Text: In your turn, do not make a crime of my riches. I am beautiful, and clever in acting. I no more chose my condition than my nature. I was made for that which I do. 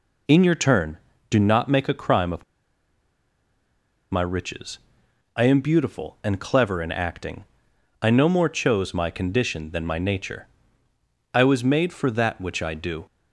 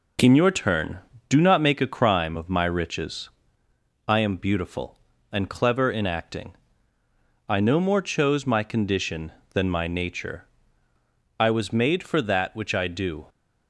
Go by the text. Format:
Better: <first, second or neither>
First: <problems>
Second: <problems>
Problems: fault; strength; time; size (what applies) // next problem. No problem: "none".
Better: second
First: pauses between "of" and "my"; strong; at 2.4 s; 1.6 s long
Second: none